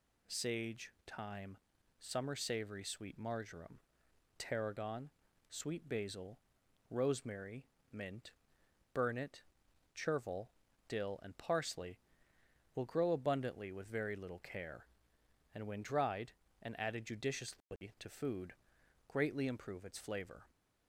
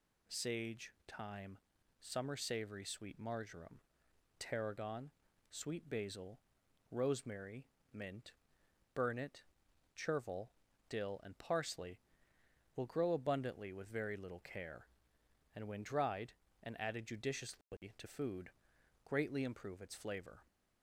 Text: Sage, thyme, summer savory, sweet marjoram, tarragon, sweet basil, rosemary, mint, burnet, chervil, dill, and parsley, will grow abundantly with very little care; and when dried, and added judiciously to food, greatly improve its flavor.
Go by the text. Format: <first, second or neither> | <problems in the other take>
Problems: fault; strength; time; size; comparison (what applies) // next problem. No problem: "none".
neither | none